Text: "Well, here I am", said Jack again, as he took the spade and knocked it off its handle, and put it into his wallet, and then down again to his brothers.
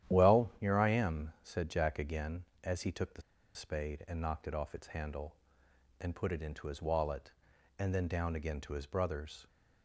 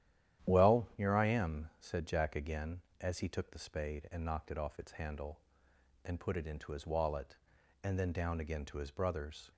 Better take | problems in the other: second | starts louder than the rest; strong; until 1.1 s; 11 dB; strong in the second // pauses between "the" and "spade"; slight; at 3.2 s; 0.33 s long

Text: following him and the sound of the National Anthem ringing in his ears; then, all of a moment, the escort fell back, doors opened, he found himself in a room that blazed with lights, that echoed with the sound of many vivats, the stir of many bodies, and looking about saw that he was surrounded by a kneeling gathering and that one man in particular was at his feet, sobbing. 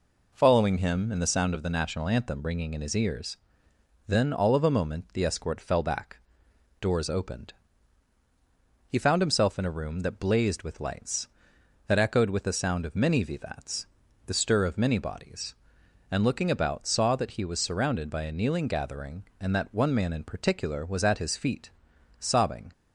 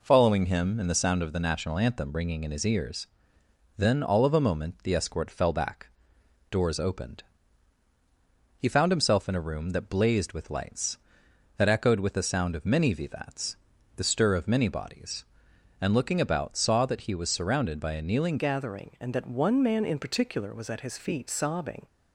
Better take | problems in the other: first | changes voice at "gathering"; from 18.3 s on; 3.5 s long

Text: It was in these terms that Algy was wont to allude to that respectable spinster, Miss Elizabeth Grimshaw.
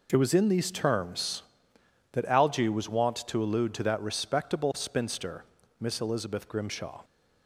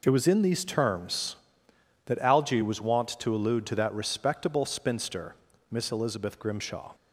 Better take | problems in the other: neither | none

